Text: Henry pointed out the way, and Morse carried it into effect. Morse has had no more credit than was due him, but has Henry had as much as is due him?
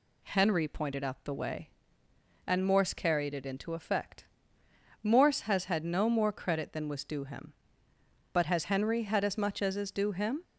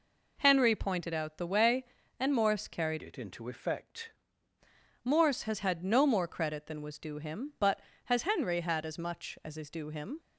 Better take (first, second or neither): first